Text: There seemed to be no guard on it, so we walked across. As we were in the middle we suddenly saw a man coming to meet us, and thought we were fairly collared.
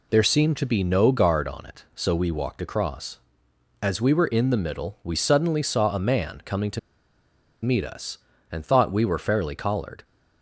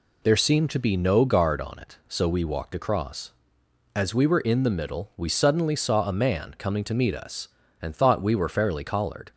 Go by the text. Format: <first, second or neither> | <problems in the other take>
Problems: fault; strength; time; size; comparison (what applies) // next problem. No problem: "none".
second | pauses between "to" and "meet"; noticeable; at 6.7 s; 0.84 s long